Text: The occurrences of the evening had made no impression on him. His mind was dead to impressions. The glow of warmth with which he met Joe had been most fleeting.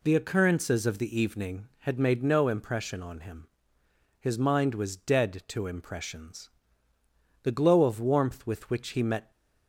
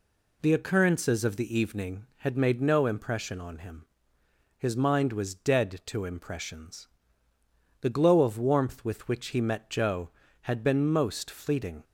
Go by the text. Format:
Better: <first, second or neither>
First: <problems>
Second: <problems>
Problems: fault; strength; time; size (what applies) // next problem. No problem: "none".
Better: second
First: stops before "Joe had been most fleeting"; at 9.3 s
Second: none